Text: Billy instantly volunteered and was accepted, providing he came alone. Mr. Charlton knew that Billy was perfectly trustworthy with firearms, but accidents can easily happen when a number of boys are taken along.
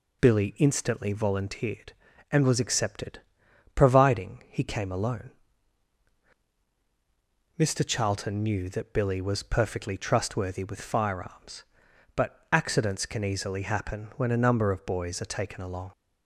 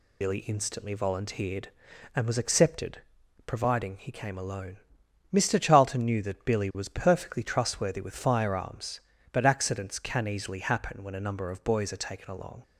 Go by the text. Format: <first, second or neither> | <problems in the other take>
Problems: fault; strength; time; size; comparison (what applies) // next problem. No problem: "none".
first | loses the start of "Billy"; at 0.2 s; 60 ms